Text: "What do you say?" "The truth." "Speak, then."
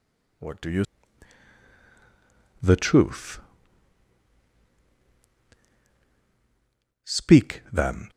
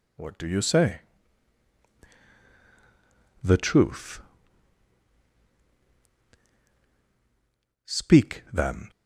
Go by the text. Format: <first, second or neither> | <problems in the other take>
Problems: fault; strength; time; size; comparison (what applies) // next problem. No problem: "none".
second | skips "say"; at 1.7 s